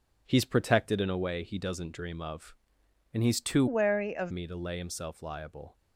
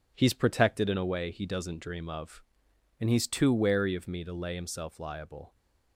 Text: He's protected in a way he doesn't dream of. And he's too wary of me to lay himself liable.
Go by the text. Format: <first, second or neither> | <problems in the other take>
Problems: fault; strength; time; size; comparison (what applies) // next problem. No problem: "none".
second | changes voice from "wary" to "of"; from 3.6 to 4.3 s; 0.7 s long